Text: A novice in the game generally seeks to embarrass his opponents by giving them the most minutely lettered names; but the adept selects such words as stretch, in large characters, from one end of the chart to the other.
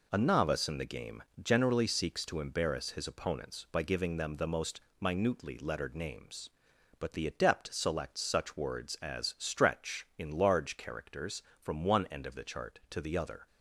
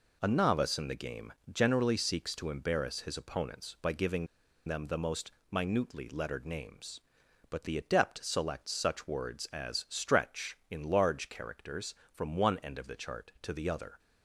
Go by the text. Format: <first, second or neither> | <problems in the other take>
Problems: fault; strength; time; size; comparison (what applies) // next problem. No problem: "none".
first | pauses between "game" and "generally"; slight; at 1.3 s; 0.18 s long; slight in the first // pauses between "giving" and "them"; at 4.2 s; 0.40 s long // pauses between "most" and "minutely"; slight; at 5.3 s; 0.22 s long; slight in the first